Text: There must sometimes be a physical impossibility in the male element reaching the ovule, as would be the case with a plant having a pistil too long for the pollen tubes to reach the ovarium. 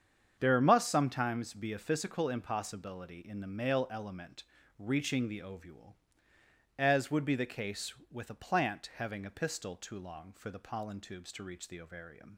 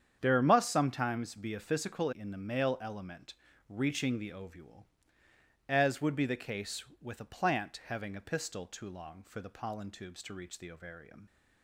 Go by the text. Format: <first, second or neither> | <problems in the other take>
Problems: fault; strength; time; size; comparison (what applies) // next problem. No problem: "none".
first | starts louder than the rest; strong; until 1.2 s; 8 dB; strong in the first // skips "impossibility"; at 2.1 s // pauses between "element" and "reaching"; slight; at 3.3 s; 0.34 s long; slight in the first